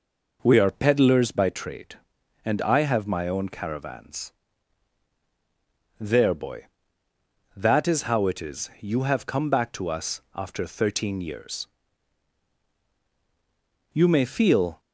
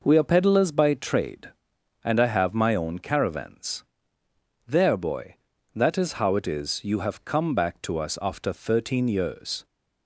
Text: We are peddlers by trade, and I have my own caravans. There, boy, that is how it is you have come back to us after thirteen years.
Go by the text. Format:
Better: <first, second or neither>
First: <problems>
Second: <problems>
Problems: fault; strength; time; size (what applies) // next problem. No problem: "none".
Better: second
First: goes on to say "You may feel"; noticeable; from 13.9 s on; 0.88 s long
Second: none